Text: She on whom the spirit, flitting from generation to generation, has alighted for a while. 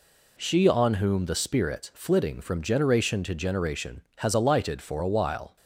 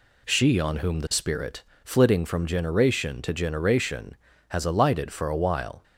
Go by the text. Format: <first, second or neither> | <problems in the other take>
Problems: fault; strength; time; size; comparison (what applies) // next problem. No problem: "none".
neither | none